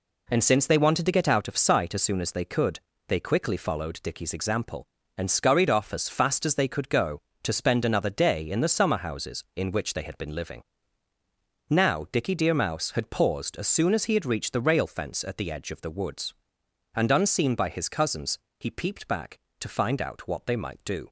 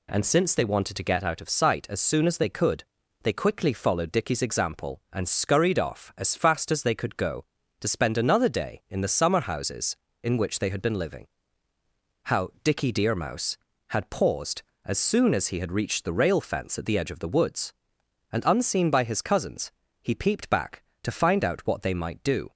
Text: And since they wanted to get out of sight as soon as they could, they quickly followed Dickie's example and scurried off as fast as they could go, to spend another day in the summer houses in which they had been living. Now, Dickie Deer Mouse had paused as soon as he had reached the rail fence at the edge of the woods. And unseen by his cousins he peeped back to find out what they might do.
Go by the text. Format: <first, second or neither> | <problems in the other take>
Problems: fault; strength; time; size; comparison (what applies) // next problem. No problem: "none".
first | says "How" for "Now"; at 12.2 s // pauses between "cousins" and "he"; slight; at 19.7 s; 0.30 s long; slight in the first